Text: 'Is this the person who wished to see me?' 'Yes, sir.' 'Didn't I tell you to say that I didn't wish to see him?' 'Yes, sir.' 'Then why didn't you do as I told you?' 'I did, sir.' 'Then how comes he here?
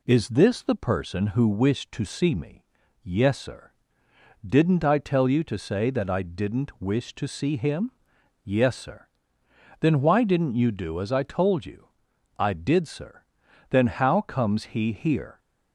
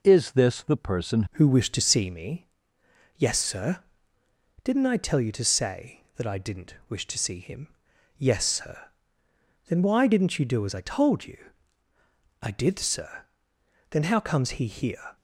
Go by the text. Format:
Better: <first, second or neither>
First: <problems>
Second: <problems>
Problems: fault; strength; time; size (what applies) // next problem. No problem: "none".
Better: first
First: none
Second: changes voice at "who"; from 1.3 s on; 13.8 s long // pauses between "didn't" and "wish"; slight; at 6.7 s; 0.16 s long